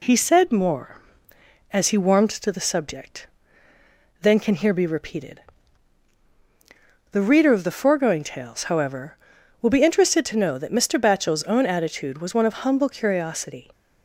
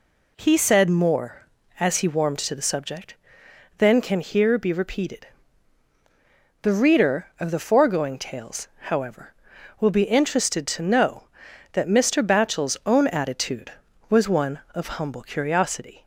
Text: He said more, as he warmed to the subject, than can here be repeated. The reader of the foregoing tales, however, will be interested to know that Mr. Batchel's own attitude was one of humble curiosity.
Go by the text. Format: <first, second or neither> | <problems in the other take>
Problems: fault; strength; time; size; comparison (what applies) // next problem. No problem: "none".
neither | none